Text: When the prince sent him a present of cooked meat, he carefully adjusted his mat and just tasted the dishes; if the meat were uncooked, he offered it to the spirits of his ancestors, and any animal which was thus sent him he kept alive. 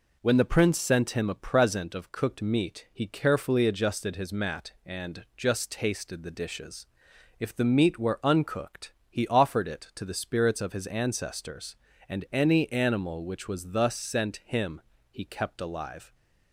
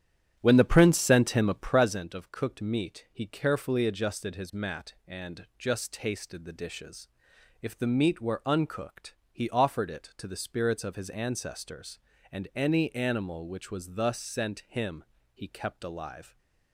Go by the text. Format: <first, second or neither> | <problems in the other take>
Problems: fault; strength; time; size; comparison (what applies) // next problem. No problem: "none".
first | starts louder than the rest; strong; until 2.0 s; 10.5 dB // pauses between "him" and "he"; slight; at 15.0 s; 0.30 s long; slight in the first